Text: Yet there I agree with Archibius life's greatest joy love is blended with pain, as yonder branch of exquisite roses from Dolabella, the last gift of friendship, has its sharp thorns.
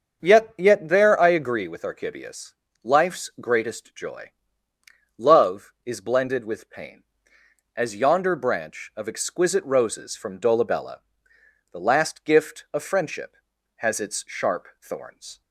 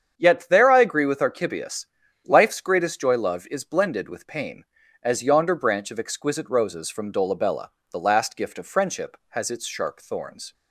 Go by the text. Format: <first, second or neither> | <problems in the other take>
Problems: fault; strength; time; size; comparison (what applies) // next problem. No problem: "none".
second | starts louder than the rest; until 1.2 s; 6.5 dB; strong in the second // says "Yet" twice; at 0.5 s // pauses between "Archibius" and "life's"; slight; at 2.5 s; 0.30 s long; also in the second // pauses between "joy" and "love"; noticeable; at 4.3 s; 0.86 s long